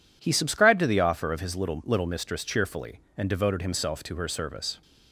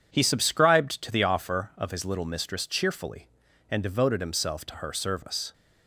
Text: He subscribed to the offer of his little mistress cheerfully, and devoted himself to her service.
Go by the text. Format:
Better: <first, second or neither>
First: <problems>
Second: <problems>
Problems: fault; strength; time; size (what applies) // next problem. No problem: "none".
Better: second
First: says "little" twice; at 1.8 s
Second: none